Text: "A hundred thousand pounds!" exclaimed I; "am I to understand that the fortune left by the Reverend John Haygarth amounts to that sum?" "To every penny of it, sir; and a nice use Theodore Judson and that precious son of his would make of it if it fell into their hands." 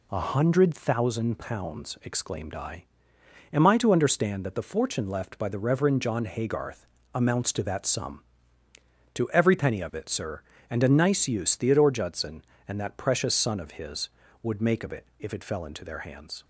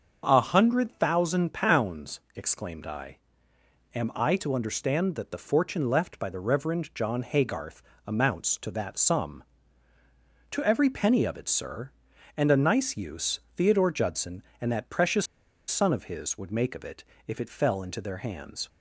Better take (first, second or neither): first